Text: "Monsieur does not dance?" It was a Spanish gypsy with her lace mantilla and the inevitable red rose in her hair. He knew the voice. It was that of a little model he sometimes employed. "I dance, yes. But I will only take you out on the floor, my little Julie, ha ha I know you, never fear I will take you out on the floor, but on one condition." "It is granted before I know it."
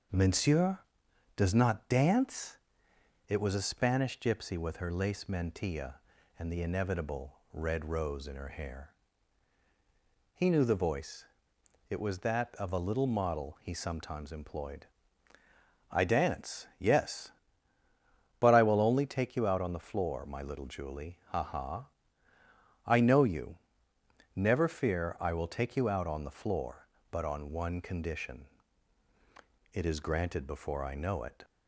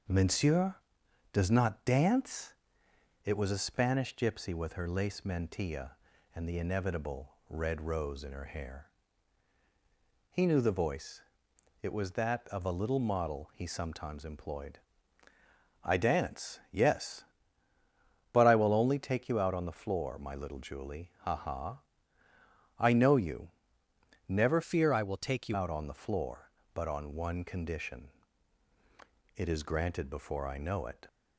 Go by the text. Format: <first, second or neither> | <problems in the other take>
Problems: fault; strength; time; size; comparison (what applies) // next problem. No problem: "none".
first | starts louder than the rest; until 1.6 s; 6.5 dB; also in the first // pauses between "ha" and "I"; noticeable; at 21.8 s; 0.98 s long; noticeable in the first // changes voice from "fear" to "you"; from 24.6 to 25.5 s; 0.9 s long